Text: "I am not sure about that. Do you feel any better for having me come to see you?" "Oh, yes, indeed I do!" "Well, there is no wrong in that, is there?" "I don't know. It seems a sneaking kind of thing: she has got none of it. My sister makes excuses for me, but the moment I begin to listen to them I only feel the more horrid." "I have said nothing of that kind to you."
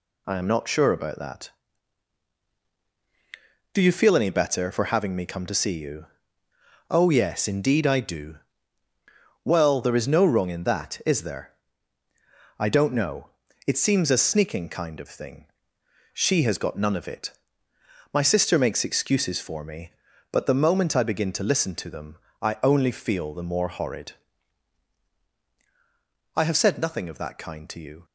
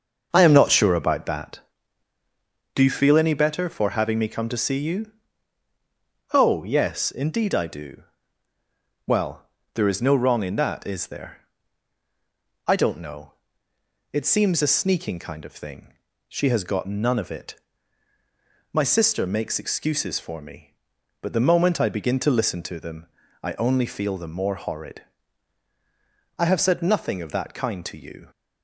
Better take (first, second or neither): first